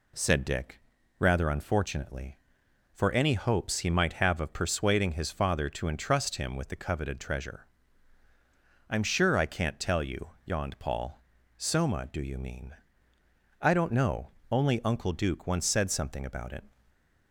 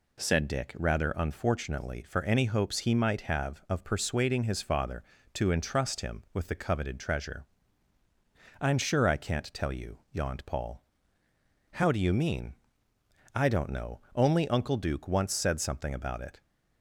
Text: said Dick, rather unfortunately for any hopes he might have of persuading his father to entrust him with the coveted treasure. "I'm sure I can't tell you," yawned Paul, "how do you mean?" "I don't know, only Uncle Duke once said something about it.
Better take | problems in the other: second | says "soma" for "how"; at 11.5 s // stays silent after the last word; slight; from 16.7 s on; 0.6 s long

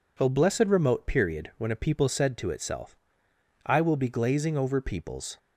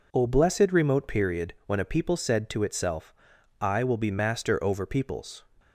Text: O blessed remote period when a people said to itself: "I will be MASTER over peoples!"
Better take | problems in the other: second | says "Glazing" for "MASTER"; at 4.0 s

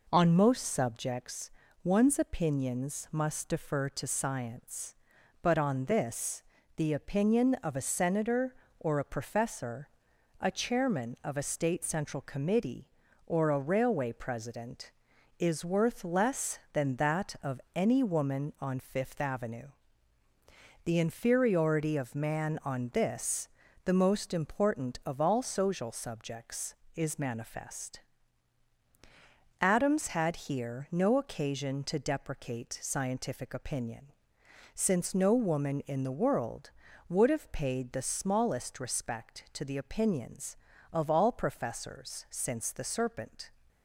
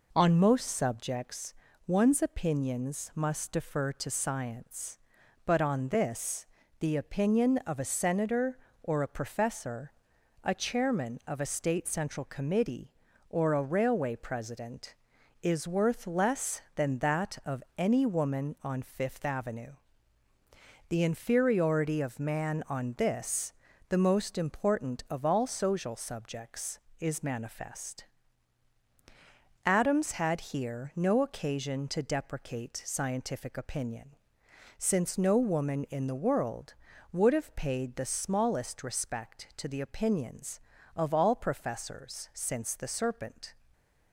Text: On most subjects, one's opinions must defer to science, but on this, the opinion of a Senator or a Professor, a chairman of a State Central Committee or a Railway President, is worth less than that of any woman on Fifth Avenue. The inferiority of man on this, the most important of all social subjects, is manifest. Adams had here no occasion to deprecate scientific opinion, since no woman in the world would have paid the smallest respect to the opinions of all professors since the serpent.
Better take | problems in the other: neither | pauses between "of" and "any"; slight; the same in both

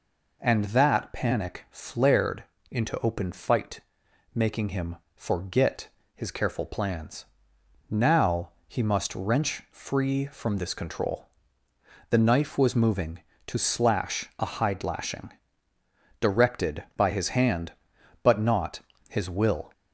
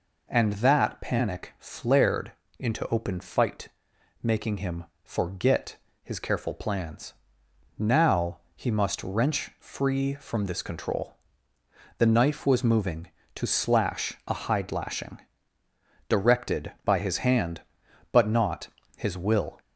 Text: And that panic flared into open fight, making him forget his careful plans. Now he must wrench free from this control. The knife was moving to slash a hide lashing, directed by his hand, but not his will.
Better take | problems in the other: neither | pauses between "flared" and "into"; slight; the same in both // pauses between "him" and "forget"; slight; the same in both // pauses between "forget" and "his"; slight; the same in both // pauses between "Now" and "he"; slight; the same in both // pauses between "not" and "his"; slight; the same in both

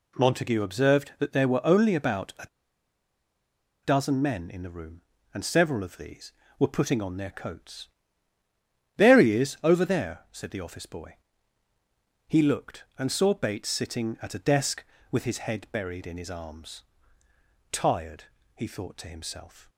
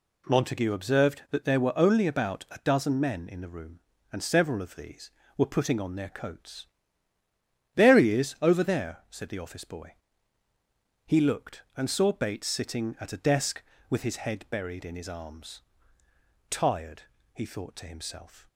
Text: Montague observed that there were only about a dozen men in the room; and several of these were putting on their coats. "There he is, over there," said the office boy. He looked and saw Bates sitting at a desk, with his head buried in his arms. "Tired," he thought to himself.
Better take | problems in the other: second | pauses between "a" and "dozen"; strong; at 2.4 s; 1.3 s long

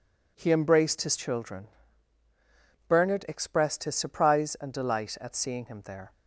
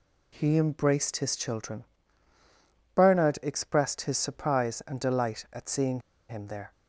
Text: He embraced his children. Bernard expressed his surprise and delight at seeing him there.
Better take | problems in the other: first | pauses between "seeing" and "him"; slight; at 5.9 s; 0.29 s long

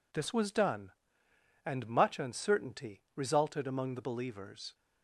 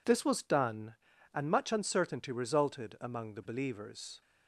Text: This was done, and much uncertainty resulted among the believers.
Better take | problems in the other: neither | none

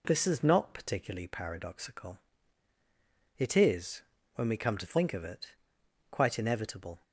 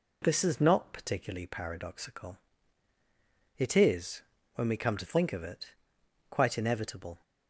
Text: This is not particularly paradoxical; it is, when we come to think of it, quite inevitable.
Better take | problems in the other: neither | none

